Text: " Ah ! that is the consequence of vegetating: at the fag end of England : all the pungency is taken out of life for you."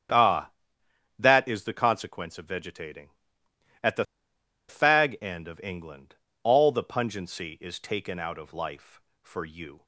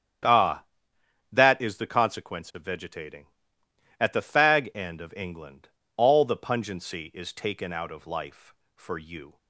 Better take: second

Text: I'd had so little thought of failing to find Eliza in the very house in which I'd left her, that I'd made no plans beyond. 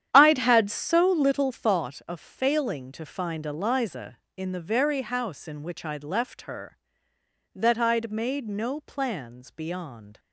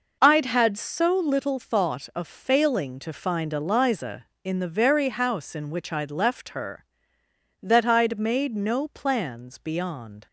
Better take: second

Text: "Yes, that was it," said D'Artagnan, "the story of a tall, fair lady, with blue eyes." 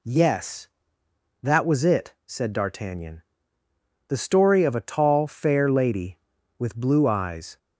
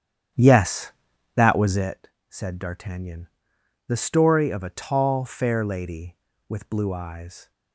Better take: first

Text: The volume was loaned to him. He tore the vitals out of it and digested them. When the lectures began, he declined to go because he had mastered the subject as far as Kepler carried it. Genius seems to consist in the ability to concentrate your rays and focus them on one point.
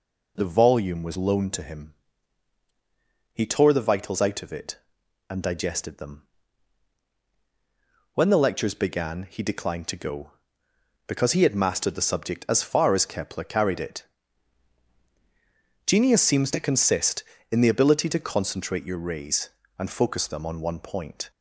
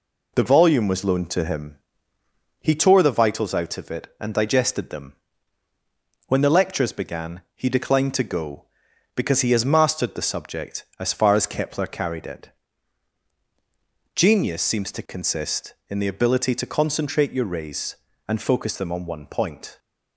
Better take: first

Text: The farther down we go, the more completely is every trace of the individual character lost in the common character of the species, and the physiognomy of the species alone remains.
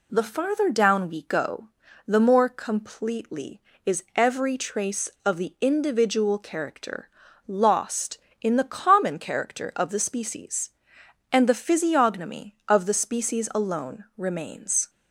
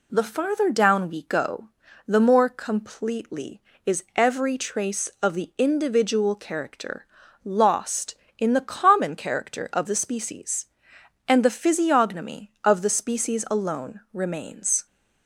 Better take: neither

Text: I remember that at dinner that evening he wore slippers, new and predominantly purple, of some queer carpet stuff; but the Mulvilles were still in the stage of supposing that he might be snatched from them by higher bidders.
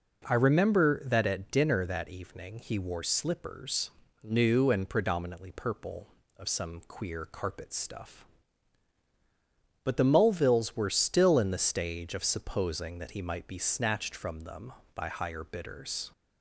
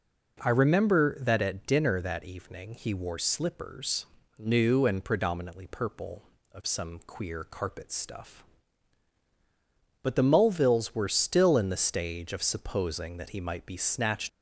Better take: first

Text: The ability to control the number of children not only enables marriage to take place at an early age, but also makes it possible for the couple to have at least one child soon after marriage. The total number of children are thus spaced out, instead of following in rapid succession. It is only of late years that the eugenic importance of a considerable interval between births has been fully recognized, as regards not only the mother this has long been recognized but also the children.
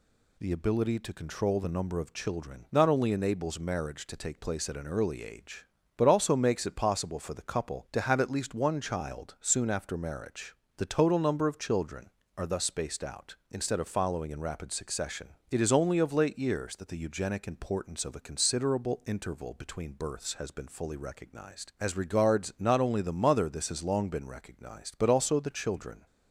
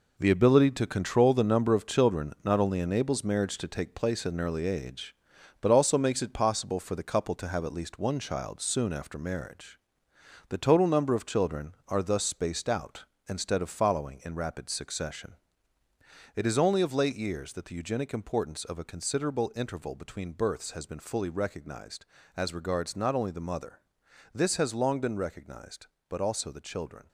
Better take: first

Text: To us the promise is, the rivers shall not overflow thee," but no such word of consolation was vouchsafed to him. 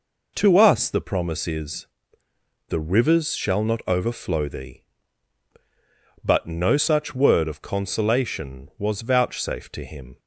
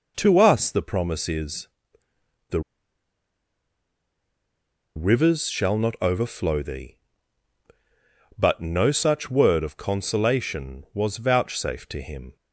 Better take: first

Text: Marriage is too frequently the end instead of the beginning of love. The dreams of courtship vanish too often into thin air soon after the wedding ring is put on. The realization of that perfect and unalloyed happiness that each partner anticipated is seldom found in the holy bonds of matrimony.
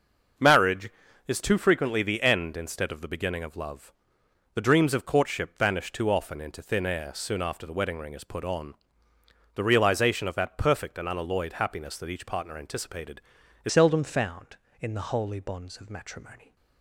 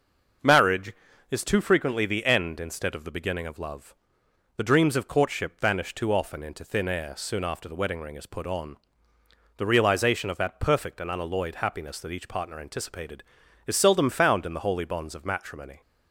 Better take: second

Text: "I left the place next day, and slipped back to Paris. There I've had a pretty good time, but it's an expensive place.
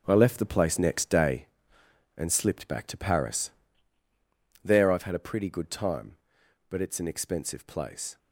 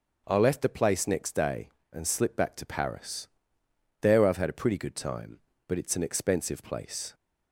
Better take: second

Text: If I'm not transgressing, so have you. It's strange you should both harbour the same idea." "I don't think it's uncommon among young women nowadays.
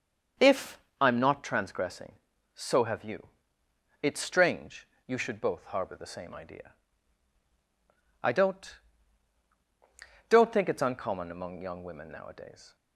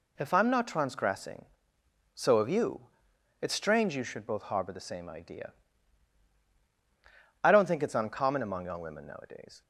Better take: second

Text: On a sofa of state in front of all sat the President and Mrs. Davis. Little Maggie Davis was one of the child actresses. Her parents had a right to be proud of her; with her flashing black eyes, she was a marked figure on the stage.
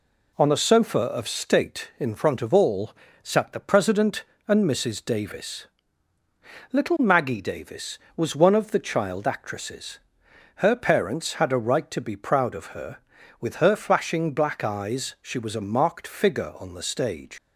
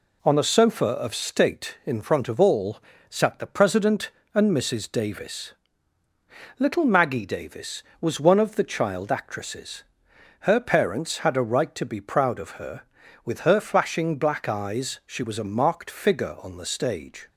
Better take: second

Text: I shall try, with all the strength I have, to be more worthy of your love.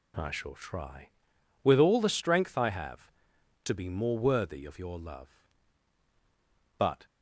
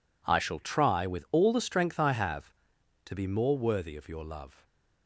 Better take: second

